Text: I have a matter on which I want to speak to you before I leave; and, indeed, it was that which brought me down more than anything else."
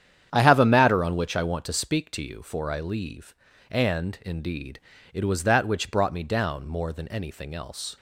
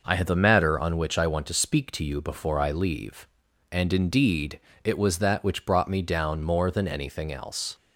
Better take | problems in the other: second | starts louder than the rest; strong; until 1.3 s; 9 dB // says "for" for "before"; at 2.4 s

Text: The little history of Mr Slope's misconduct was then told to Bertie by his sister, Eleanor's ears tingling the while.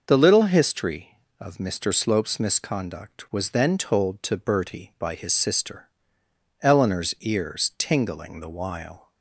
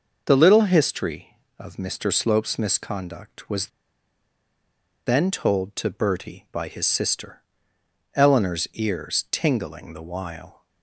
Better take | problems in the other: first | pauses between "was" and "then"; strong; at 3.6 s; 1.3 s long

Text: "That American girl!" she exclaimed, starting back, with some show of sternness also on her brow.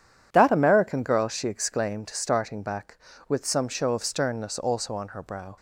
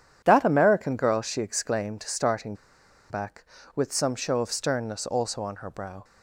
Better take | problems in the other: first | pauses between "starting" and "back"; noticeable; at 2.5 s; 0.55 s long

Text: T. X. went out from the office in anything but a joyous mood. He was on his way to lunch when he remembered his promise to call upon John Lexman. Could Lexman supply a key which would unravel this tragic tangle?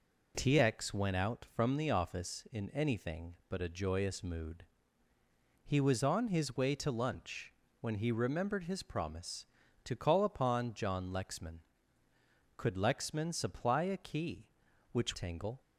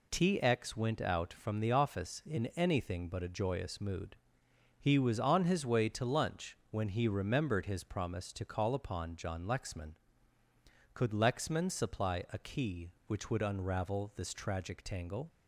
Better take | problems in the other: second | pauses between "lunch" and "when"; slight; at 7.5 s; 0.26 s long; slight in the second // skips "would unravel this tragic"; at 15.1 s

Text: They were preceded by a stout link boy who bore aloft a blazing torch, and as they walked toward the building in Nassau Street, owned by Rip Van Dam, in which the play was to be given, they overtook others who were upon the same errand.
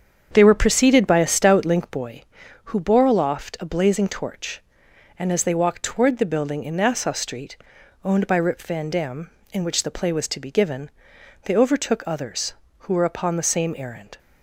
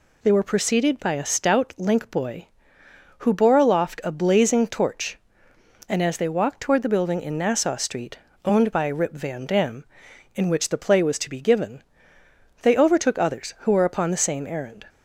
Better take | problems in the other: second | starts louder than the rest; strong; until 2.1 s; 7.5 dB

